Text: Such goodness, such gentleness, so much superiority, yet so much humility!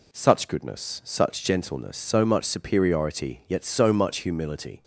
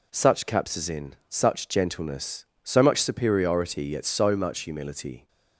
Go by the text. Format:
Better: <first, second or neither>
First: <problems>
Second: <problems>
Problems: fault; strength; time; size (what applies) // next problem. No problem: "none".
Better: first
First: none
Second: says "capsizin" for "goodness"; at 0.4 s